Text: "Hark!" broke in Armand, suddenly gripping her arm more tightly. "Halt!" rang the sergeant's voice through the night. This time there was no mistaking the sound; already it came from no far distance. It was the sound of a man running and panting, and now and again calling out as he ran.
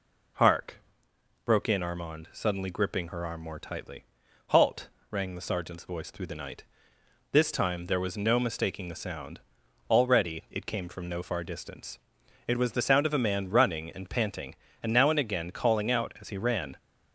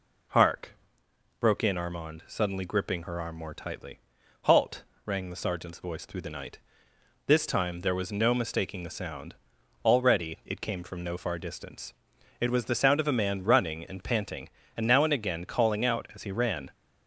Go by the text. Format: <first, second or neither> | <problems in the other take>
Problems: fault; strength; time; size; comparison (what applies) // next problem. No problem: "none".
neither | none